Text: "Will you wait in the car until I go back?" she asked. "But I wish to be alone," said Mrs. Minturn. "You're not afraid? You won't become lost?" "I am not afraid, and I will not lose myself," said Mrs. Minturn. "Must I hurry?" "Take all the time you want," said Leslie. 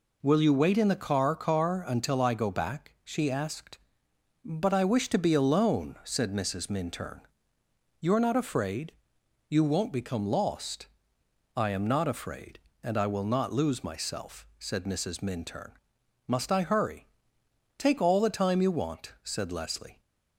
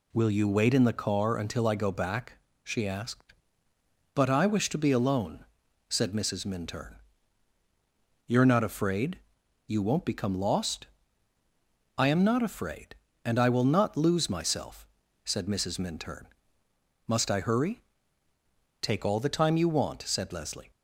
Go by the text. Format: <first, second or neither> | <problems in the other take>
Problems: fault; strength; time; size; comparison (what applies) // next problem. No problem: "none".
second | says "car" twice; at 1.3 s